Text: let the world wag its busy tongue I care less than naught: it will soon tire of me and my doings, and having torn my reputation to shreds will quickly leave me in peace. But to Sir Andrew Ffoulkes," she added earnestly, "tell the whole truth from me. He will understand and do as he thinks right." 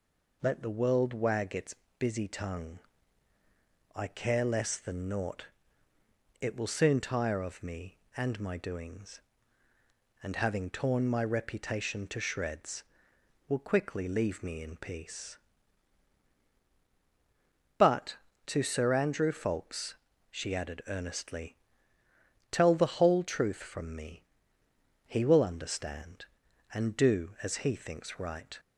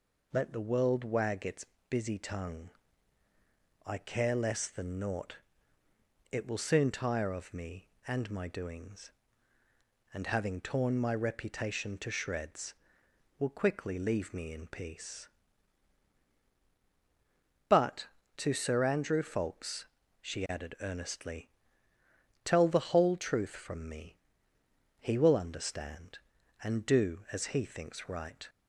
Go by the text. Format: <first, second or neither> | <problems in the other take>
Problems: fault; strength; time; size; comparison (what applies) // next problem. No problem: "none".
neither | pauses between "its" and "busy"; slight; the same in both // pauses between "tongue" and "I"; the same in both